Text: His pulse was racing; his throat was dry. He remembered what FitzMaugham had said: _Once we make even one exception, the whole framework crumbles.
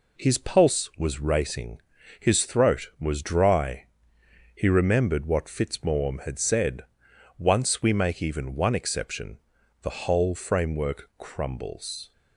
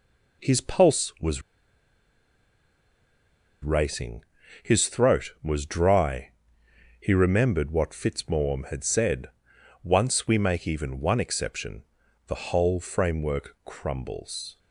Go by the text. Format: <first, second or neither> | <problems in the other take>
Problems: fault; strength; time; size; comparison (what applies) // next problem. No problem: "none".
first | pauses between "was" and "racing"; strong; at 1.4 s; 2.2 s long